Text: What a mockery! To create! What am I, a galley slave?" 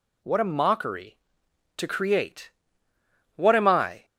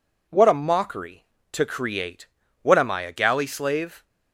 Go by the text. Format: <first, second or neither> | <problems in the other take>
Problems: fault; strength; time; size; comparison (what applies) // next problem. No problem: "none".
second | stops before "a galley slave"; at 4.0 s